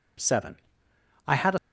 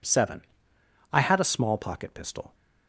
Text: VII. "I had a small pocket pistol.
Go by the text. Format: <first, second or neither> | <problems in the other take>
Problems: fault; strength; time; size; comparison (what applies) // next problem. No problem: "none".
second | stops before "small pocket pistol"; at 1.5 s